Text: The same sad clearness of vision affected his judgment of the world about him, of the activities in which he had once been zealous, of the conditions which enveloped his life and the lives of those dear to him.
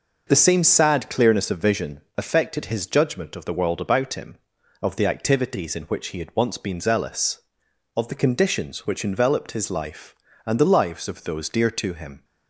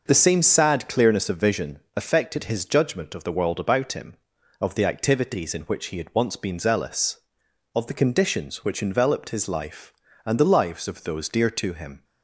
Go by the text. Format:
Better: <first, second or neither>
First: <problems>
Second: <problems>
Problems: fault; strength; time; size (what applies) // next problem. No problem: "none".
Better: neither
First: pauses between "vision" and "affected"; slight; at 2.0 s; 0.16 s long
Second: pauses between "vision" and "affected"; slight; at 1.8 s; 0.16 s long